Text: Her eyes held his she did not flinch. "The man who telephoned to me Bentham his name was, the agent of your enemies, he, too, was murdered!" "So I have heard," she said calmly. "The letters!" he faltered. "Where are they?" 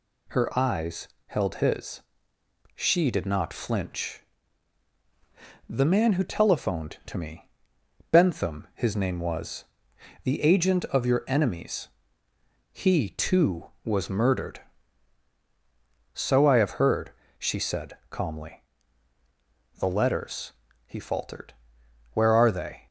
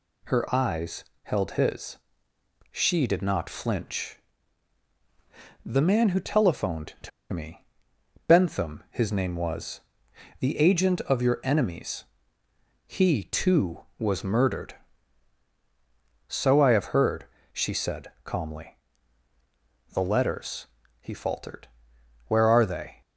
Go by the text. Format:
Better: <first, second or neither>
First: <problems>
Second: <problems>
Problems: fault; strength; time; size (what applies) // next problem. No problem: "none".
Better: first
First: pauses between "eyes" and "held"; slight; at 1.0 s; 0.20 s long // pauses between "his" and "she"; noticeable; at 2.0 s; 0.78 s long // pauses between "me" and "Bentham"; noticeable; at 7.4 s; 0.62 s long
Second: pauses between "eyes" and "held"; slight; at 1.0 s; 0.20 s long // pauses between "his" and "she"; noticeable; at 1.9 s; 0.78 s long // pauses between "to" and "me"; slight; at 7.1 s; 0.22 s long // pauses between "me" and "Bentham"; noticeable; at 7.6 s; 0.62 s long